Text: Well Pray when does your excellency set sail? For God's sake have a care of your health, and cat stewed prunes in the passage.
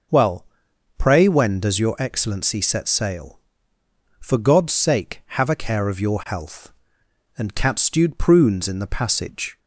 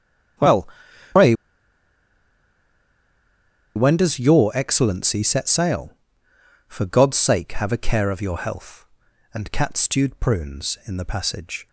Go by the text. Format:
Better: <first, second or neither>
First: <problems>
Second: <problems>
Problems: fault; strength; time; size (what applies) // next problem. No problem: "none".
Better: first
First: pauses between "Well" and "Pray"; noticeable; at 0.4 s; 0.54 s long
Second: starts louder than the rest; strong; until 4.2 s; 9.5 dB // pauses between "Well" and "Pray"; noticeable; at 0.6 s; 0.46 s long // pauses between "Pray" and "when"; strong; at 1.3 s; 2.4 s long